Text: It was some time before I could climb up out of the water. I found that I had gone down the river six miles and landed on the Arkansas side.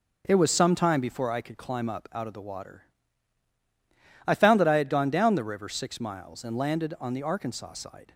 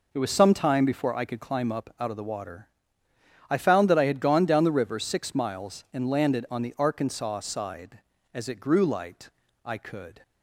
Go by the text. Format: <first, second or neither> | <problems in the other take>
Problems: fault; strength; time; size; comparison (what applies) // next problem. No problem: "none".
first | goes on to say "As it grew light I could"; strong; from 8.3 s on; 1.9 s long